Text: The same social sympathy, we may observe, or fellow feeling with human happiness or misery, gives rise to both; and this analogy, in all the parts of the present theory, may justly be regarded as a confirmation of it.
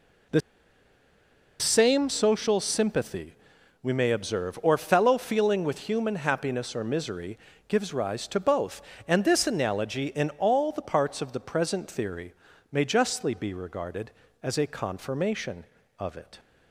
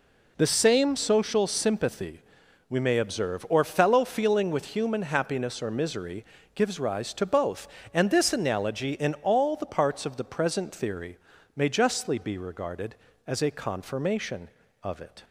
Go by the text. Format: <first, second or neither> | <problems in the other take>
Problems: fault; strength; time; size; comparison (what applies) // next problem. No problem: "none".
second | pauses between "The" and "same"; at 0.4 s; 1.1 s long